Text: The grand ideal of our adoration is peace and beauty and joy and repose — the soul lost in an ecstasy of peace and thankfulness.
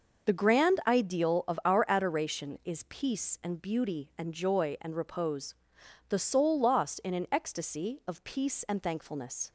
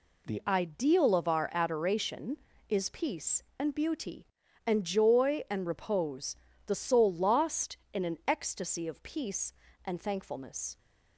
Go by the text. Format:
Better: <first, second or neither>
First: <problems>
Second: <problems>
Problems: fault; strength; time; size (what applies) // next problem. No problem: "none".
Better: first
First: none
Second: skips "grand"; at 0.4 s